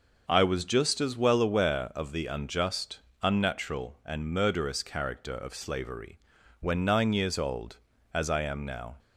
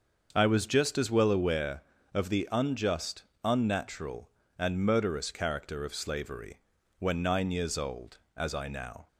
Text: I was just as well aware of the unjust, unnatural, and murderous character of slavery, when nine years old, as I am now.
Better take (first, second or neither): first